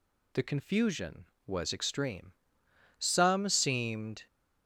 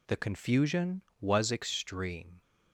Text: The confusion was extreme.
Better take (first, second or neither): second